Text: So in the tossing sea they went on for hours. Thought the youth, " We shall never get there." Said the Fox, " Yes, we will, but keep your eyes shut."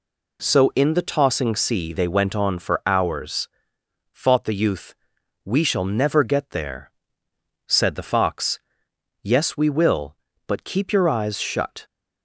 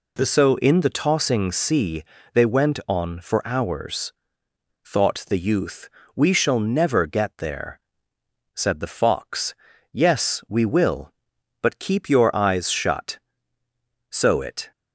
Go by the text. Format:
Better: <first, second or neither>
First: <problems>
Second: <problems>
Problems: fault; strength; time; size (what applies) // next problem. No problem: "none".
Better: first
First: none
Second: pauses between "sea" and "they"; slight; at 2.0 s; 0.30 s long // goes on to say "So it"; noticeable; from 14.0 s on; 0.62 s long